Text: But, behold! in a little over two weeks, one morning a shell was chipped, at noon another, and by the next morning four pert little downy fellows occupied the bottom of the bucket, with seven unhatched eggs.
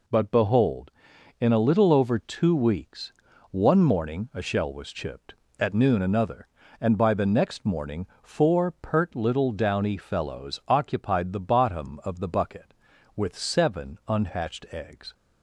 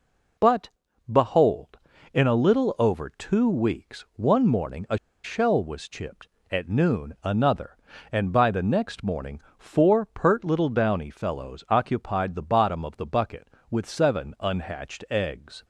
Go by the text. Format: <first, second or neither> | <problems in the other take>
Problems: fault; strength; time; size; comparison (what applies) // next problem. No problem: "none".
first | pauses between "a" and "shell"; slight; at 4.9 s; 0.26 s long // pauses between "morning" and "four"; slight; at 9.4 s; 0.16 s long; slight in the first